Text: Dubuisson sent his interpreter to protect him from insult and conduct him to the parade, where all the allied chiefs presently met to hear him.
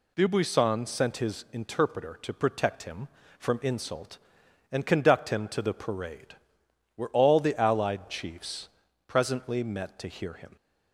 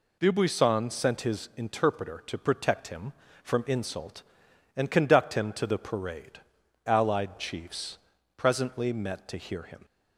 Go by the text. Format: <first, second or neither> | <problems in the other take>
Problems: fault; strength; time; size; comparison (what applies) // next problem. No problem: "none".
first | skips "where all the"; at 6.6 s // pauses between "chiefs" and "presently"; at 7.9 s; 0.40 s long; also in the first